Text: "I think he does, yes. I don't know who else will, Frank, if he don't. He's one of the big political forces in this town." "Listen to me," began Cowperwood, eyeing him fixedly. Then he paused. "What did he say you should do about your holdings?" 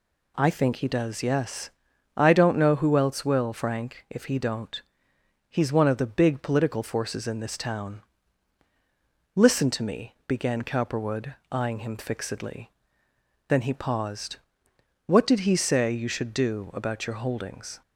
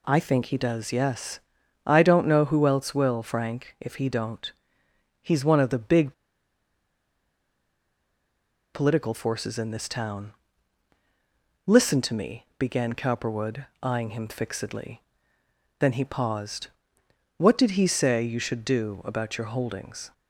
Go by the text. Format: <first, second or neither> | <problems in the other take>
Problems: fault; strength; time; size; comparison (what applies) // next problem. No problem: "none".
first | pauses between "big" and "political"; strong; at 6.1 s; 2.5 s long